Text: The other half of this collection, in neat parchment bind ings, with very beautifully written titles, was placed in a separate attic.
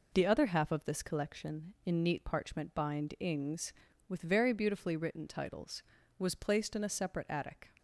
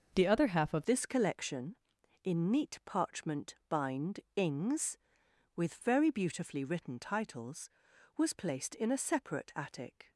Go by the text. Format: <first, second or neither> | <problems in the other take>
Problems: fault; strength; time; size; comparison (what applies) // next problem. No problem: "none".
first | starts louder than the rest; noticeable; until 1.1 s; 6 dB // changes voice at "this"; from 0.8 s on; 9.3 s long // pauses between "bind" and "ings"; slight; at 4.1 s; 0.16 s long